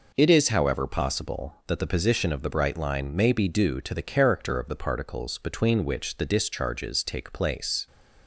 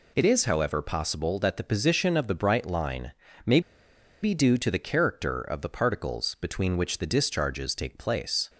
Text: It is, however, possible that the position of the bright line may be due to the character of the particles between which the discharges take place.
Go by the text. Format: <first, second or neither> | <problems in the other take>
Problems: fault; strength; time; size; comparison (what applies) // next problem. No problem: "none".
first | pauses between "line" and "may"; slight; at 3.1 s; 0.34 s long // pauses between "may" and "be"; noticeable; at 3.5 s; 0.62 s long